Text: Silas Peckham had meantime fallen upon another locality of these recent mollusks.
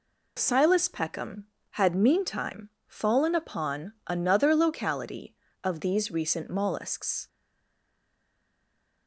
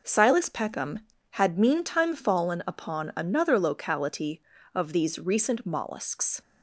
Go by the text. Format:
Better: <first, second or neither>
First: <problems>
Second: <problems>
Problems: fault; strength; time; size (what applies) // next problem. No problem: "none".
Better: second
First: pauses between "meantime" and "fallen"; slight; at 2.6 s; 0.16 s long // stays silent after the last word; noticeable; from 7.2 s on; 1.8 s long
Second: none